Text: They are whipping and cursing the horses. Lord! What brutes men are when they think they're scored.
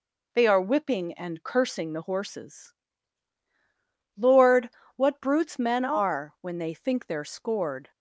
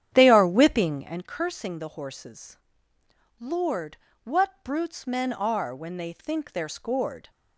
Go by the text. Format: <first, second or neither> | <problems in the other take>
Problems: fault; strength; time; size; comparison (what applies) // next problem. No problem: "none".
first | starts louder than the rest; strong; until 1.2 s; 9.5 dB